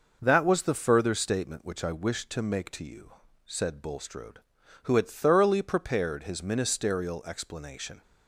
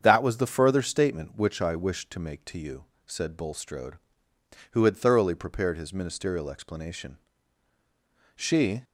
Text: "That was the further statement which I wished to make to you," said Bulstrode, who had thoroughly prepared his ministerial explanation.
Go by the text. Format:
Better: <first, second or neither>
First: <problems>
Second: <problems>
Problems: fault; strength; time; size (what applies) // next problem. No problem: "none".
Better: first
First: none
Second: starts louder than the rest; strong; until 1.0 s; 7.5 dB // goes on to say "She"; slight; from 8.3 s on; 0.48 s long